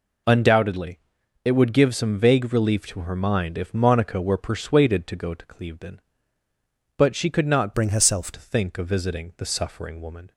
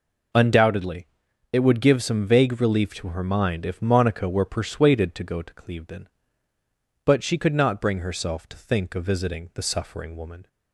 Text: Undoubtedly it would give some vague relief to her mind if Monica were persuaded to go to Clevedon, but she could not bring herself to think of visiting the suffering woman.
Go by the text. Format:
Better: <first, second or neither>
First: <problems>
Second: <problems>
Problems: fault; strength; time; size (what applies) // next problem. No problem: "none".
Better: second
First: pauses between "Undoubtedly" and "it"; noticeable; at 0.9 s; 0.46 s long // changes voice from "bring" to "herself"; from 7.7 to 8.3 s; 0.6 s long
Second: pauses between "Undoubtedly" and "it"; noticeable; at 1.0 s; 0.46 s long